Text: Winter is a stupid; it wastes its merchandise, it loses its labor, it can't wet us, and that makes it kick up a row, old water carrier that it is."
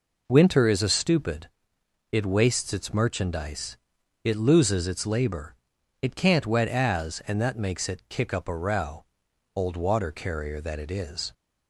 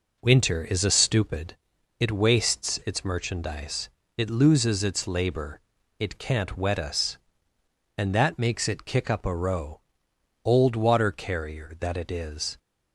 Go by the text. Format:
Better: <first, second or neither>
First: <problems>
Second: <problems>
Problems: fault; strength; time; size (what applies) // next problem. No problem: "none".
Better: second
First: says "as" for "us"; at 6.6 s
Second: none